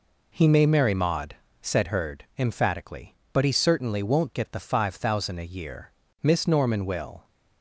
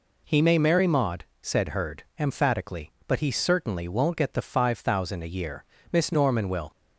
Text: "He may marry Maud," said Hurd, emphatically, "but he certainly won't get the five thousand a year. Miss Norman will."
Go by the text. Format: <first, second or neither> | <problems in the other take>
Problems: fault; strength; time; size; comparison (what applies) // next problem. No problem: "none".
neither | none